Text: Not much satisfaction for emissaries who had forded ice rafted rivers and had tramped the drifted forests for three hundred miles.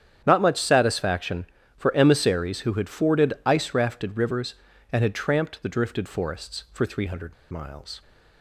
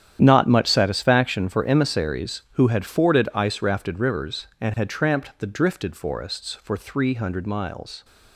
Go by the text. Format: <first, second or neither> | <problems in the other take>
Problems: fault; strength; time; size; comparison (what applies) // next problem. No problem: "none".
second | starts louder than the rest; strong; until 1.2 s; 9 dB; strong in the second // pauses between "hundred" and "miles"; slight; at 7.3 s; 0.17 s long